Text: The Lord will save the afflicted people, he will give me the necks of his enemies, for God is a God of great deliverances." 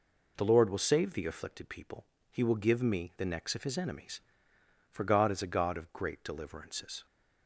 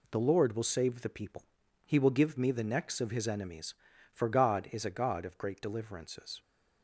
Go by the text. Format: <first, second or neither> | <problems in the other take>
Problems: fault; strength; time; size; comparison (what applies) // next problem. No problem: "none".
first | skips "afflicted"; at 1.0 s